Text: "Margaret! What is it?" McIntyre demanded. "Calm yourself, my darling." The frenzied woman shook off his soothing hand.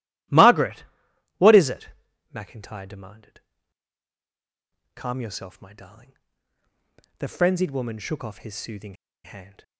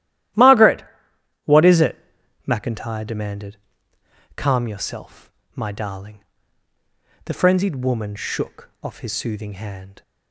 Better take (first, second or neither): second